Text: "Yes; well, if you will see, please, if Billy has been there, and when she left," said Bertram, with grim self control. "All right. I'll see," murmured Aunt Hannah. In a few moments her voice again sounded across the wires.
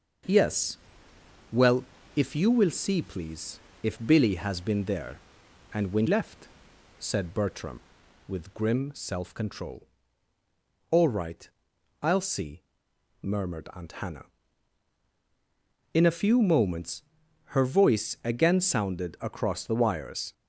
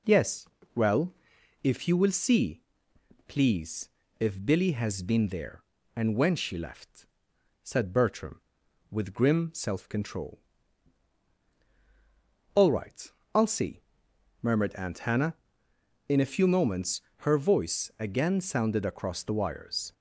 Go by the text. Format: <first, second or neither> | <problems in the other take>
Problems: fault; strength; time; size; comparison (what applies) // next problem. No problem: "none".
second | starts louder than the rest; noticeable; until 2.3 s; 6 dB // skips "she"; at 6.0 s // pauses between "moments" and "her"; noticeable; at 17.0 s; 0.50 s long; slight in the second